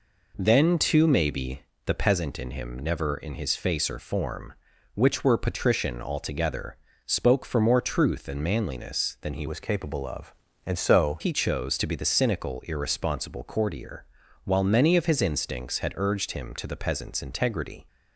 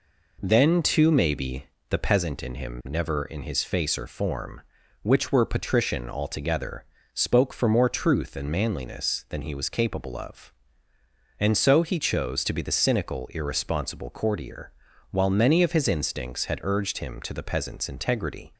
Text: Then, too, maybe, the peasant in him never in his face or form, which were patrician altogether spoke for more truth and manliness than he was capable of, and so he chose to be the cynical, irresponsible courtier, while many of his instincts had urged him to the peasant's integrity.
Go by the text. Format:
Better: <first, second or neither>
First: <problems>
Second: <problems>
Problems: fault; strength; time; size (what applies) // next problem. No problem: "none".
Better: second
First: pauses between "altogether" and "spoke"; slight; at 6.7 s; 0.30 s long // changes voice from "was" to "so"; from 9.4 to 11.1 s; 1.7 s long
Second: pauses between "altogether" and "spoke"; slight; at 6.8 s; 0.30 s long